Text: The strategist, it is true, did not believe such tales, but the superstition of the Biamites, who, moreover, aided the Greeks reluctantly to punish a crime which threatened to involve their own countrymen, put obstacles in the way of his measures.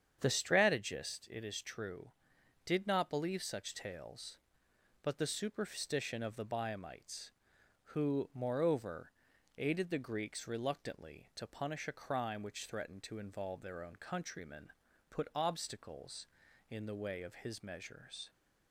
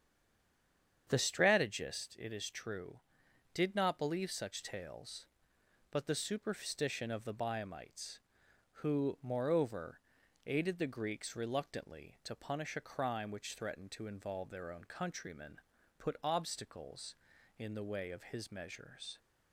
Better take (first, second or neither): first